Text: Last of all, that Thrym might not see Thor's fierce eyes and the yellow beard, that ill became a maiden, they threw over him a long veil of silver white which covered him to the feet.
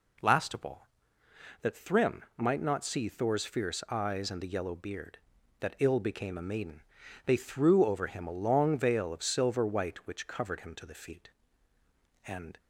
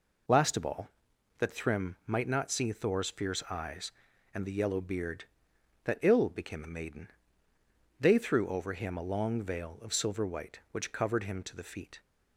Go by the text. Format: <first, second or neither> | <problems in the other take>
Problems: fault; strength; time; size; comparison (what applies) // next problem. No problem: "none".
second | goes on to say "And"; slight; from 12.2 s on; 0.32 s long